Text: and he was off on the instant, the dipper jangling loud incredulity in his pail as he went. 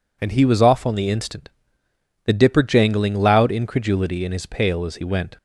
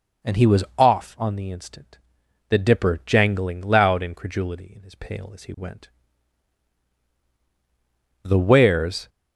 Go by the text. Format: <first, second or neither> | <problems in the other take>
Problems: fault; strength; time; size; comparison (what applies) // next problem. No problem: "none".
first | goes on to say "The Wares"; noticeable; from 8.2 s on; 0.86 s long